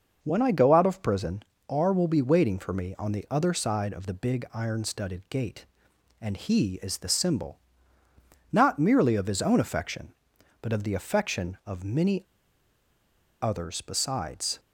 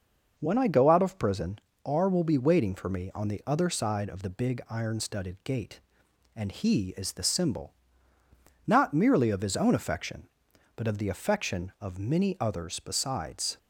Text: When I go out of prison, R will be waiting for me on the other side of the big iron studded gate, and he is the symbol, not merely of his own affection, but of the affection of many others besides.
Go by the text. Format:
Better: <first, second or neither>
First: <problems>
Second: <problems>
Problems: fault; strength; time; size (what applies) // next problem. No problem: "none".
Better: second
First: pauses between "many" and "others"; at 12.2 s; 1.1 s long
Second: none